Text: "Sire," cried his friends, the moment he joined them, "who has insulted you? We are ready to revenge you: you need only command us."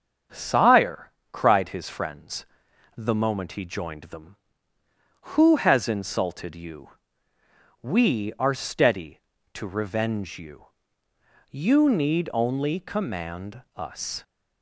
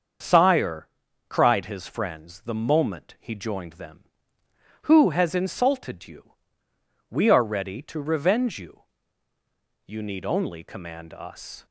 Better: second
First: starts louder than the rest; strong; until 1.5 s; 7.5 dB // says "steady" for "ready"; at 8.5 s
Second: starts louder than the rest; until 1.6 s; 6.5 dB

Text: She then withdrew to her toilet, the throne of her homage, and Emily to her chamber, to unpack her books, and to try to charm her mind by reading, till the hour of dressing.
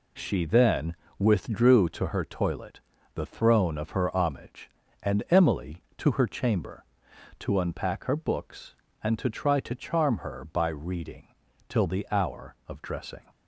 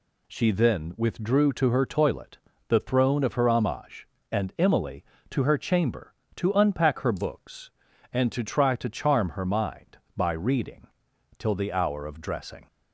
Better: second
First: pauses between "then" and "withdrew"; slight; at 0.9 s; 0.24 s long // skips "mind"; at 10.4 s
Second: none

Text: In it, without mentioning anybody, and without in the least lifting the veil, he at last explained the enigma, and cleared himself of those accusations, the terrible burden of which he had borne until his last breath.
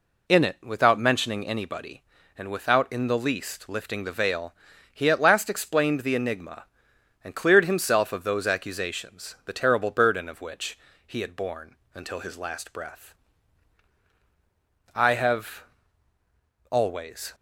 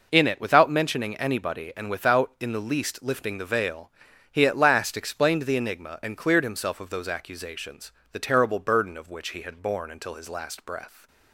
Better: second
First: pauses between "which" and "he"; slight; at 10.7 s; 0.28 s long // pauses between "borne" and "until"; slight; at 11.7 s; 0.18 s long // goes on to say "I have always"; strong; from 14.9 s on; 2.4 s long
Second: none

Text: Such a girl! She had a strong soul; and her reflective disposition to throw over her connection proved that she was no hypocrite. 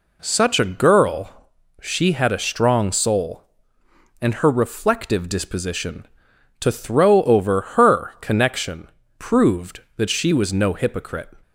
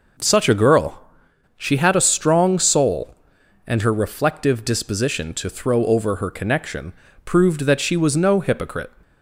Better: neither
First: pauses between "connection" and "proved"; slight; at 8.8 s; 0.28 s long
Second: pauses between "connection" and "proved"; slight; at 6.9 s; 0.32 s long

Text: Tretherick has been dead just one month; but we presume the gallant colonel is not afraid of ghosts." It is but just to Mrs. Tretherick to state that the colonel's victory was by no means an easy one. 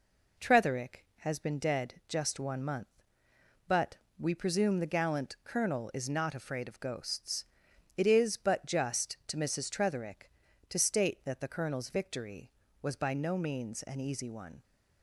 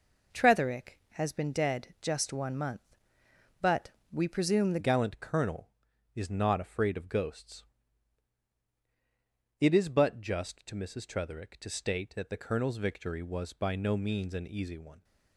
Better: first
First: pauses between "but" and "we"; slight; at 3.9 s; 0.22 s long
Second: pauses between "but" and "we"; slight; at 3.9 s; 0.22 s long // changes voice at "gallant"; from 4.7 s on; 10.3 s long

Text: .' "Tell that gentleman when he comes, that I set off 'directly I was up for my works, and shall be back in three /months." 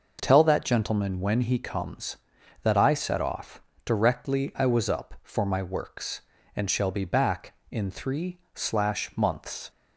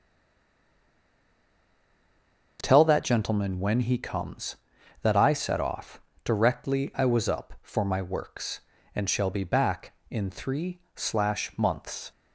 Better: first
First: pauses between "off" and "directly"; slight; at 3.6 s; 0.24 s long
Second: stays silent before the first word; strong; until 2.5 s; 2.5 s long // pauses between "off" and "directly"; slight; at 6.0 s; 0.24 s long

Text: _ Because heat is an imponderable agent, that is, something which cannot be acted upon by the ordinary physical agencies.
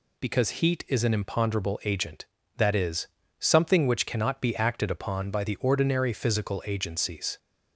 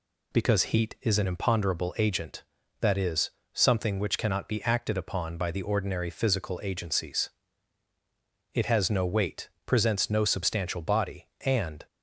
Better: first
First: none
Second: goes on to say "It has no weight presents no substantial body and"; strong; from 8.5 s on; 3.3 s long

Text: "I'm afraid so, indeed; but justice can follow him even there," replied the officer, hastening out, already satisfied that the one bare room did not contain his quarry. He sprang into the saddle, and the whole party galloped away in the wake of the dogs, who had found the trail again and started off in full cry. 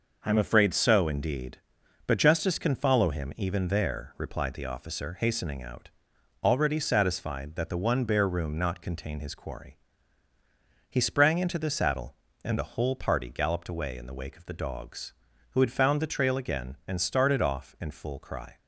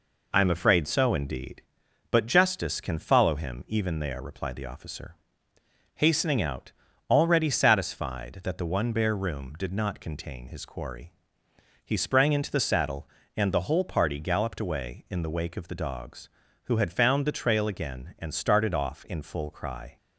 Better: second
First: skips "did"; at 8.5 s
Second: none

